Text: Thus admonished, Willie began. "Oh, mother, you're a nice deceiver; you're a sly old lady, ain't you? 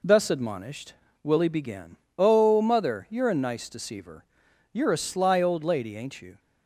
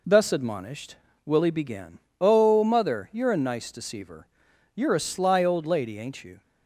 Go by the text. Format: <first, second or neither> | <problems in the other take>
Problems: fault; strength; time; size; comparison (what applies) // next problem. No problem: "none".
neither | none